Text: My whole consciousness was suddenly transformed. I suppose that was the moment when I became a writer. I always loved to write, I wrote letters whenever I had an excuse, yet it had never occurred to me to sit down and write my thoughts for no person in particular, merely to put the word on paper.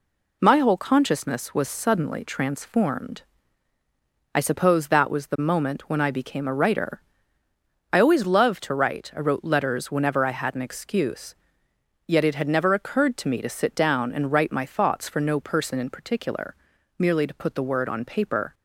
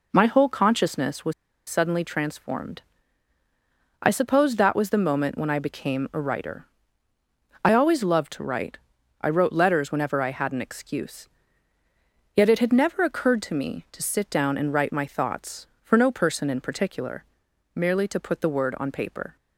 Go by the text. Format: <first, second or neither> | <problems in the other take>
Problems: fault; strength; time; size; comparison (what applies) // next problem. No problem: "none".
first | pauses between "was" and "suddenly"; at 1.3 s; 0.36 s long